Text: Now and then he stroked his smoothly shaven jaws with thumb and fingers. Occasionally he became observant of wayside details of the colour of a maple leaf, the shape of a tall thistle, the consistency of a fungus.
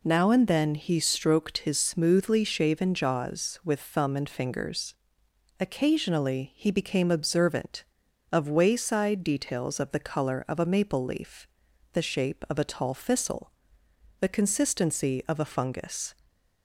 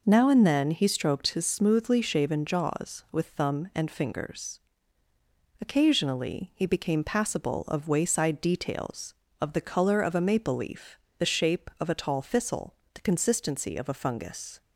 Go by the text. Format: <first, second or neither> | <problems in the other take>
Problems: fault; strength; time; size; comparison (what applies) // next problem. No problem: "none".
first | says "passable" for "observant"; at 7.0 s